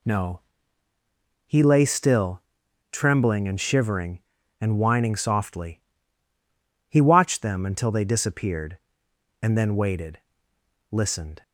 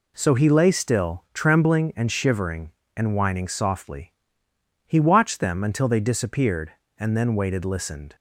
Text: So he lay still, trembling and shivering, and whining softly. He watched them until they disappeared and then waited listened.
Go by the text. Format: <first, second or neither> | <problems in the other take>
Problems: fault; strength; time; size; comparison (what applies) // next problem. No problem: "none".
second | says "No" for "So"; at 0.0 s // pauses between "waited" and "listened"; noticeable; at 10.1 s; 0.76 s long